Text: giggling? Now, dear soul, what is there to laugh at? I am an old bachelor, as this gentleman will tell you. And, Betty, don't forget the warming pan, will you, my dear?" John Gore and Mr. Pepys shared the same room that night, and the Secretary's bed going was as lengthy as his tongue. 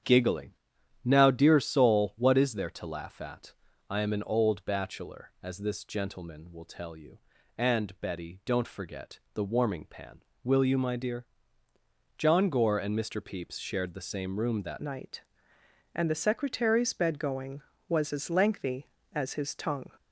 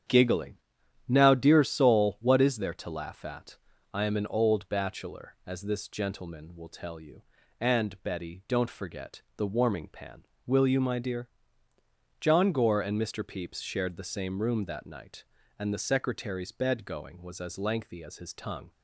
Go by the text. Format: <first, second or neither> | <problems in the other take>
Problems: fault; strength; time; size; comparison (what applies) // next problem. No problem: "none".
second | starts louder than the rest; strong; until 1.5 s; 9 dB; strong in the second // changes voice at "night"; from 14.8 s on; 5.0 s long